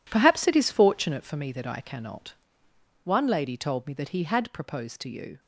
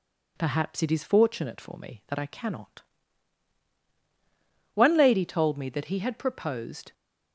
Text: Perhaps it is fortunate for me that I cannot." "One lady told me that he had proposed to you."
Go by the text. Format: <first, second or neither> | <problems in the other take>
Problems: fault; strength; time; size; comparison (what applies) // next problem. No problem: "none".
first | stops before "to you"; at 6.9 s